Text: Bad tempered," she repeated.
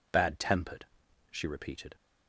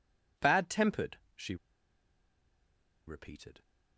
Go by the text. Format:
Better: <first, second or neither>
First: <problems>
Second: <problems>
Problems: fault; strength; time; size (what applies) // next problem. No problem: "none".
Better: first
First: none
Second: pauses between "she" and "repeated"; strong; at 1.5 s; 1.5 s long